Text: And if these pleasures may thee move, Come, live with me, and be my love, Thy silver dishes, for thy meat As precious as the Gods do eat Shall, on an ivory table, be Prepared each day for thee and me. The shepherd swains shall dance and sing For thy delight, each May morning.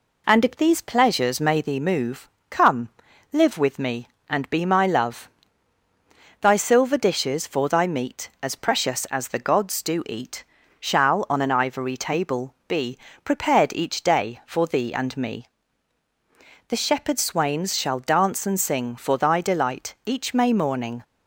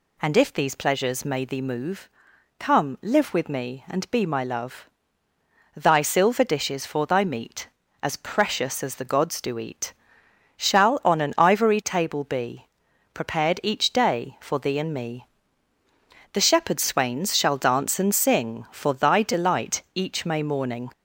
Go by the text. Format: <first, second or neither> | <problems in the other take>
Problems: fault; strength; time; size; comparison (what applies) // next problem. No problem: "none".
first | gets louder; slight; throughout; 3 dB // pauses between "eat" and "Shall"; noticeable; at 9.9 s; 0.62 s long; slight in the first // pauses between "be" and "Prepared"; noticeable; at 12.6 s; 0.48 s long; slight in the first